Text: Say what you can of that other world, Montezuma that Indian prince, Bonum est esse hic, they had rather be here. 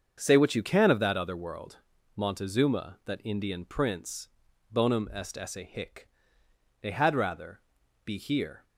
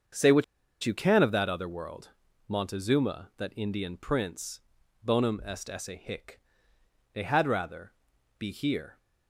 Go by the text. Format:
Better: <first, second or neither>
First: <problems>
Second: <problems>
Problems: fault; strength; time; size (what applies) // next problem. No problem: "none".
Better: first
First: starts louder than the rest; until 1.1 s; 6.5 dB // pauses between "rather" and "be"; noticeable; at 7.5 s; 0.46 s long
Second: starts louder than the rest; until 1.5 s; 6.5 dB // pauses between "what" and "you"; at 0.4 s; 0.39 s long // pauses between "rather" and "be"; noticeable; at 7.9 s; 0.48 s long